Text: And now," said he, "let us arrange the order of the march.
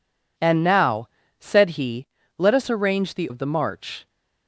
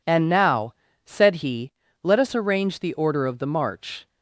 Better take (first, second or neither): second